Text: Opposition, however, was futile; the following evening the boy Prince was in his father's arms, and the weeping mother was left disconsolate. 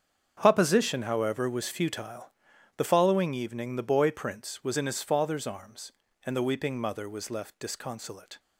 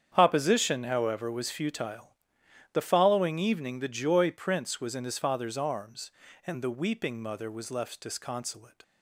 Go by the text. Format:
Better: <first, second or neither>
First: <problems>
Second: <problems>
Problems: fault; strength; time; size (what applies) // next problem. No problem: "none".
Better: first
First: starts louder than the rest; strong; until 1.4 s; 7.5 dB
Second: starts louder than the rest; strong; until 1.1 s; 8 dB // says "joy" for "boy"; at 3.8 s